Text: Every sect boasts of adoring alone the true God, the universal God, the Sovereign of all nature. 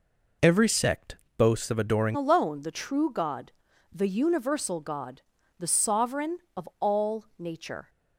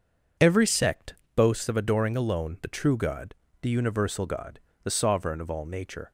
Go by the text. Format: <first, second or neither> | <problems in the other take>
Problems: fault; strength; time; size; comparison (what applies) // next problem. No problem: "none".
second | pauses between "sect" and "boasts"; slight; at 1.1 s; 0.18 s long; slight in the second // changes voice at "alone"; from 2.1 s on; 5.7 s long